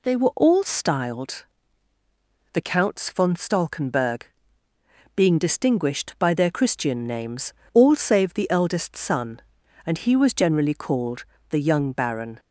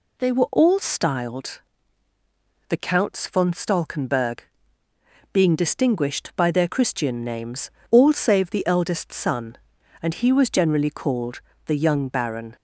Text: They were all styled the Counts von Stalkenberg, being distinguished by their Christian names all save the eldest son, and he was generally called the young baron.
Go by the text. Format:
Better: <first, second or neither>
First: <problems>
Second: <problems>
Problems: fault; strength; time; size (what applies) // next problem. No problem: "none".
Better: neither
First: pauses between "styled" and "the"; at 1.4 s; 1.0 s long // pauses between "names" and "all"; slight; at 7.5 s; 0.22 s long // pauses between "called" and "the"; slight; at 11.2 s; 0.24 s long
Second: pauses between "styled" and "the"; at 1.6 s; 1.0 s long // pauses between "names" and "all"; slight; at 7.6 s; 0.22 s long // pauses between "called" and "the"; slight; at 11.4 s; 0.24 s long